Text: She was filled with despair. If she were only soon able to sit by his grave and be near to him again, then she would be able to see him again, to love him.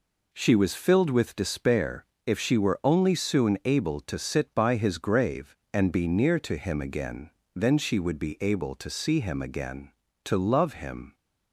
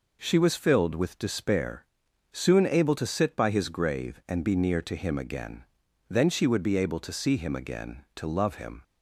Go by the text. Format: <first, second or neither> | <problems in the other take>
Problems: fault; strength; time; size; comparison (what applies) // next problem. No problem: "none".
first | skips "If she were only"; at 2.0 s